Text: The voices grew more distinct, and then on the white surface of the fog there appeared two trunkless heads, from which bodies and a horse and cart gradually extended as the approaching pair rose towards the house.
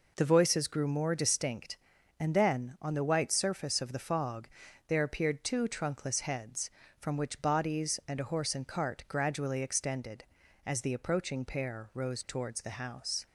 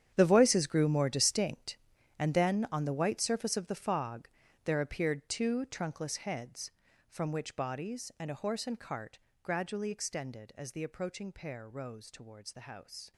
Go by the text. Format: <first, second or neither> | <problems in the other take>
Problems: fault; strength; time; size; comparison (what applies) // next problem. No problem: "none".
first | gets quieter; strong; throughout; 15 dB // pauses between "fog" and "there"; slight; at 4.2 s; 0.36 s long; also in the first // pauses between "cart" and "gradually"; slight; at 9.1 s; 0.26 s long